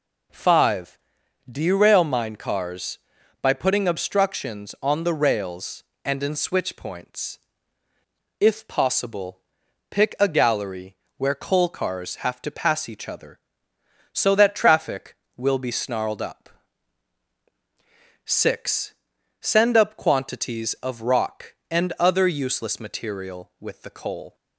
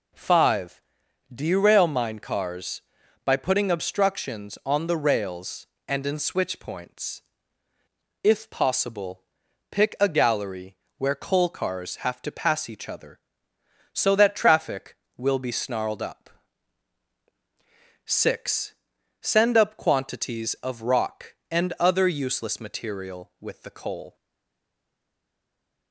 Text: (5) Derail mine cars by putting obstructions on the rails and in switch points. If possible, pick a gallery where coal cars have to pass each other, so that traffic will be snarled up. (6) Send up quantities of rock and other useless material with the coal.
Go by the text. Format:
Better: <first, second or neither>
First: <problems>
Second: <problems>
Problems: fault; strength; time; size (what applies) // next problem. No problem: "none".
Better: first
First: pauses between "gallery" and "where"; slight; at 10.9 s; 0.22 s long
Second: pauses between "gallery" and "where"; slight; at 10.7 s; 0.22 s long // stays silent after the last word; noticeable; from 24.1 s on; 1.8 s long